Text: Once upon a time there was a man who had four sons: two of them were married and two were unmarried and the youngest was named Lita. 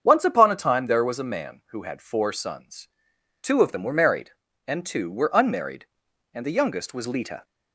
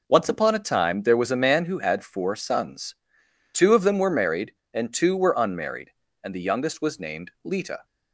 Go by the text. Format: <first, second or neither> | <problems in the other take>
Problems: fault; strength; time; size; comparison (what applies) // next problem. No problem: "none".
second | starts louder than the rest; strong; until 1.0 s; 7.5 dB // skips "named"; at 7.0 s